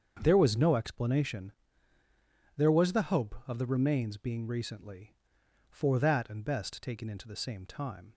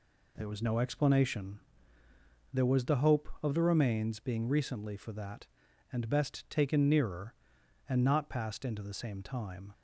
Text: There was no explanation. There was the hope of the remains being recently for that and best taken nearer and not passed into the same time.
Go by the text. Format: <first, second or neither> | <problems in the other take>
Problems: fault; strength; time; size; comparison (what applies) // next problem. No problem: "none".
second | starts louder than the rest; strong; until 1.2 s; 7 dB // skips "nearer and not passed"; at 7.0 s